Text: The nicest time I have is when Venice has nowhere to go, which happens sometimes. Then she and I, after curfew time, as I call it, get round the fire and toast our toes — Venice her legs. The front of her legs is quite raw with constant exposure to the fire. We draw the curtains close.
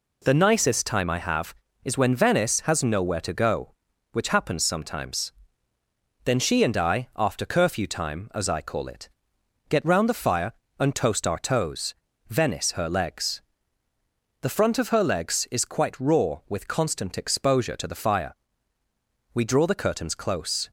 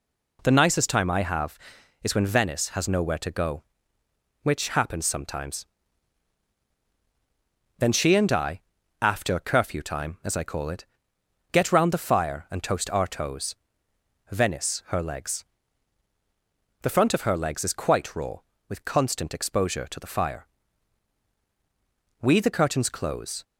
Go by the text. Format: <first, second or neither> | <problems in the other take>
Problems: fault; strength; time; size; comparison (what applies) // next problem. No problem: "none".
first | skips "draw"; at 22.3 s